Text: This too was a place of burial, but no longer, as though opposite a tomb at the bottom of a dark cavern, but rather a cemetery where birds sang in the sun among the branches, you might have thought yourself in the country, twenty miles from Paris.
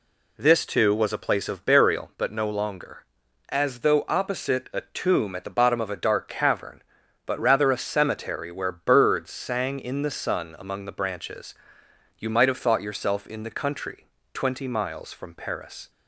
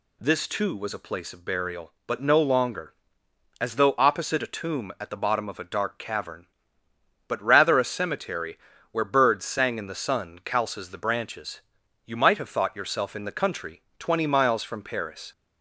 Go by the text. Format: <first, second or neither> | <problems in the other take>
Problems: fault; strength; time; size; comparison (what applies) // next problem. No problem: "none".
first | pauses between "cemetery" and "where"; slight; at 8.5 s; 0.34 s long // says "calces" for "among"; at 10.4 s